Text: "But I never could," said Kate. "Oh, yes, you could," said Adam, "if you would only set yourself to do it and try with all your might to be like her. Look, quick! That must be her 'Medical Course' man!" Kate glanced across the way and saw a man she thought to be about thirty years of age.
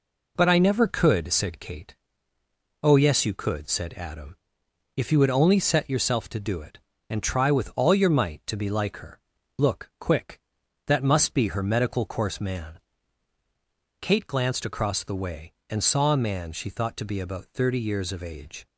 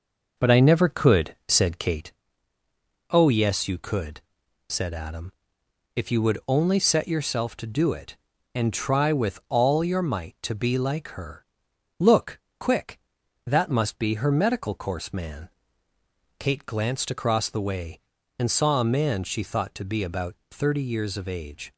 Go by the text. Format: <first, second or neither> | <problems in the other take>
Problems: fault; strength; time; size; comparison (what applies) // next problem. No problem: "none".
first | starts louder than the rest; noticeable; until 2.2 s; 5.5 dB // pauses between "about" and "thirty"; slight; at 20.3 s; 0.16 s long